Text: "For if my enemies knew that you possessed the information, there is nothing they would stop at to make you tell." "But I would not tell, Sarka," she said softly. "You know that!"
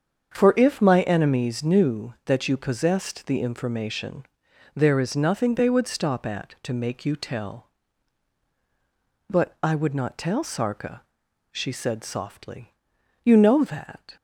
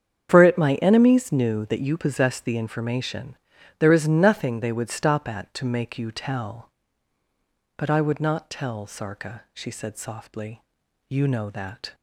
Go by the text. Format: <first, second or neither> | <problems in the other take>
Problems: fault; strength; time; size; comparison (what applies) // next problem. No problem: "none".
first | starts louder than the rest; strong; until 1.3 s; 8 dB; strong in the first // says "it" for "if"; at 0.4 s